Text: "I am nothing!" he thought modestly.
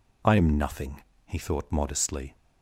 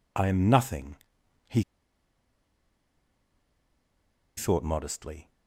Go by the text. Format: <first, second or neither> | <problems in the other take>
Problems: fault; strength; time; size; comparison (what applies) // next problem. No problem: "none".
first | pauses between "he" and "thought"; strong; at 1.6 s; 2.7 s long